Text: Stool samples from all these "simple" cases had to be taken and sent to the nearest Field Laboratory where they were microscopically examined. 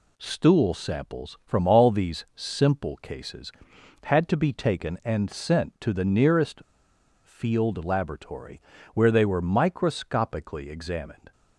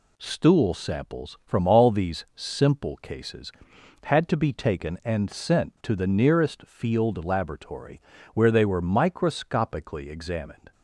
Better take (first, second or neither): second